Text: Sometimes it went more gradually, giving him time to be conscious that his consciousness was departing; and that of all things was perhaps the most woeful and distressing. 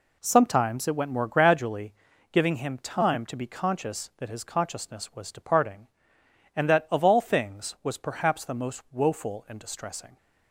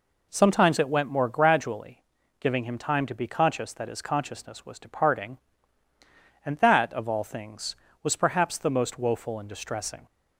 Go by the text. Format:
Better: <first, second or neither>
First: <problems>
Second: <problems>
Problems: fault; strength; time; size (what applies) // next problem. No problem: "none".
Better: neither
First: none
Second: none